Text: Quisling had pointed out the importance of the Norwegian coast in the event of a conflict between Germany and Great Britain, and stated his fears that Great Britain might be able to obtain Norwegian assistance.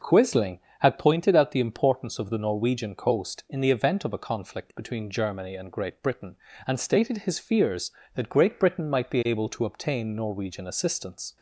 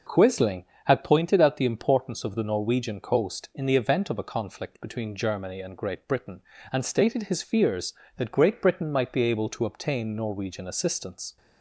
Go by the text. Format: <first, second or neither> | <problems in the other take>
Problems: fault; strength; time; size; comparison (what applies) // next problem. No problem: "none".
neither | none